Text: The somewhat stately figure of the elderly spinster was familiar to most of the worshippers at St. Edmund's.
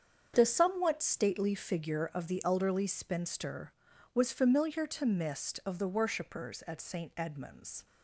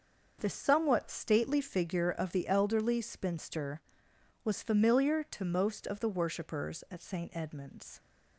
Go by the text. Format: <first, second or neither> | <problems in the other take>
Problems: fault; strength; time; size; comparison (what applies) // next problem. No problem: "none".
second | starts louder than the rest; strong; until 1.3 s; 7.5 dB; also in the second // says "mist" for "most"; at 5.0 s